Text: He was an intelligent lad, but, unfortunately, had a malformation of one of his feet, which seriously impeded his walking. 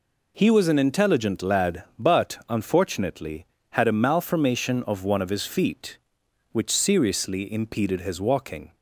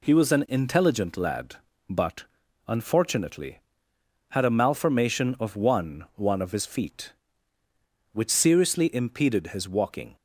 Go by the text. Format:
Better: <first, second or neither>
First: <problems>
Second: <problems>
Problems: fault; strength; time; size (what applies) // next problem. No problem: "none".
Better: first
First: none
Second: says "one" twice; at 6.1 s